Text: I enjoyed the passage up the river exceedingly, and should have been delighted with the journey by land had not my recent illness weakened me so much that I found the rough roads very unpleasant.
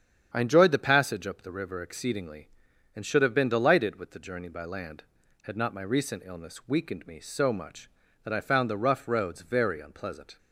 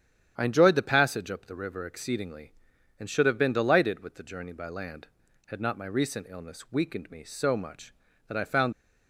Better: first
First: starts louder than the rest; strong; until 1.3 s; 8.5 dB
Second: starts louder than the rest; strong; until 1.3 s; 9.5 dB // stops before "the rough roads very unpleasant"; at 8.7 s

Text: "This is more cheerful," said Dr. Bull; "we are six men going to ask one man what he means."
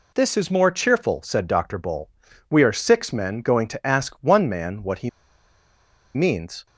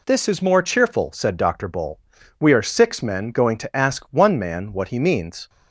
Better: second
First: pauses between "he" and "means"; at 5.0 s; 1.0 s long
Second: none

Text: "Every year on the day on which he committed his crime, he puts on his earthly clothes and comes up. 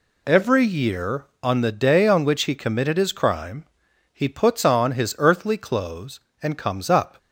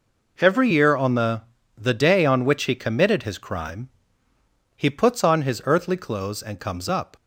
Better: first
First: none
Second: says "the" twice; at 1.7 s

